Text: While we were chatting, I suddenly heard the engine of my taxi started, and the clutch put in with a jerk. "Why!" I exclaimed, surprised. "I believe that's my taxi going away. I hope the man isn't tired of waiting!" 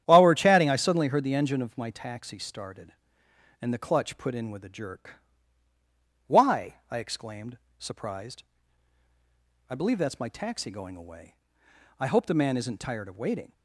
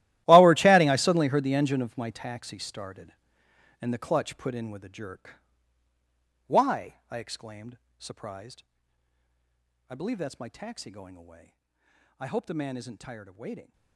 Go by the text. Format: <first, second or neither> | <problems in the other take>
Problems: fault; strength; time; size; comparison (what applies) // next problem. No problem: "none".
first | gets quieter; strong; throughout; 18 dB // starts louder than the rest; strong; until 1.2 s; 15 dB; strong in the first